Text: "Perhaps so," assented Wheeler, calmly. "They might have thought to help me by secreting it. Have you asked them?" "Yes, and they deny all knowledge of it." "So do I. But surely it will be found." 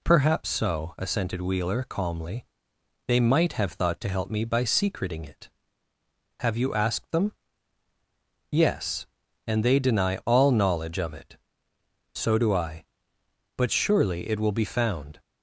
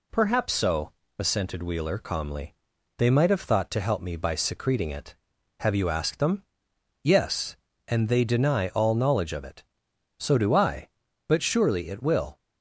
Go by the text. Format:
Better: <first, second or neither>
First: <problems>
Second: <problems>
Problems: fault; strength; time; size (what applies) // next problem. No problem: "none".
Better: first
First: none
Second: stops before "be found"; at 12.3 s